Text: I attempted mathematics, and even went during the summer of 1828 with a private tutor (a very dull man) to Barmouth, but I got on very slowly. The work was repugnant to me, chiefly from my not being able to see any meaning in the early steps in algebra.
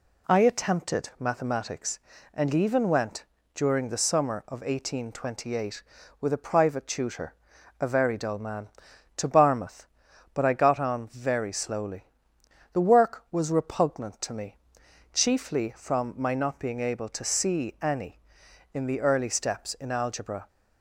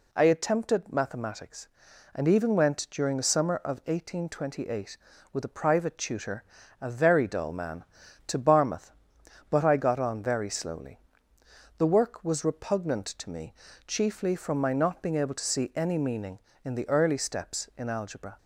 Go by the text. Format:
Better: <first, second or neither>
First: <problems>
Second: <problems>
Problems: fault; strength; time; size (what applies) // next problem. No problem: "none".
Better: second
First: pauses between "went" and "during"; slight; at 3.2 s; 0.28 s long // skips "meaning"; at 18.4 s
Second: none